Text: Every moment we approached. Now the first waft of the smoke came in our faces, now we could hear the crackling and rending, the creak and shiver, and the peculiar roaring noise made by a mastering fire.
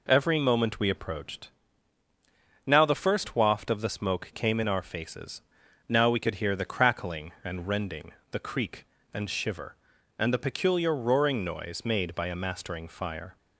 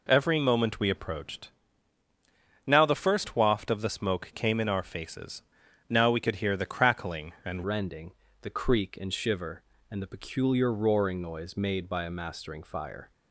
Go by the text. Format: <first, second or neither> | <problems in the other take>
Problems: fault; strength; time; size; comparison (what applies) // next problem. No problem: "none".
first | changes voice at "rending"; from 7.6 s on; 5.5 s long